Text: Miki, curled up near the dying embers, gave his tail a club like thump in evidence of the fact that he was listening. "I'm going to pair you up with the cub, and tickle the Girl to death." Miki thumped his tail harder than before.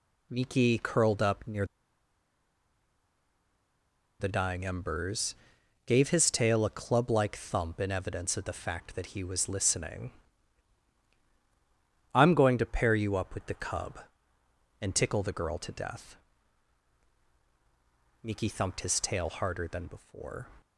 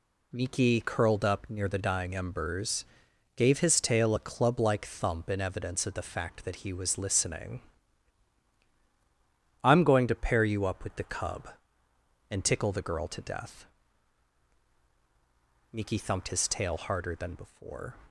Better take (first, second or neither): second